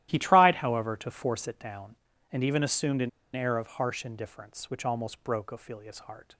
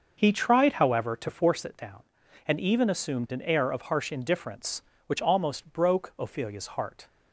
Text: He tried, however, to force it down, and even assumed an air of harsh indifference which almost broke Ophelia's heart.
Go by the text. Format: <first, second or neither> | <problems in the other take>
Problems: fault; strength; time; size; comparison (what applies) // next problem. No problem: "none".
second | starts louder than the rest; strong; until 1.1 s; 13.5 dB; also in the second // pauses between "an" and "air"; slight; at 3.0 s; 0.25 s long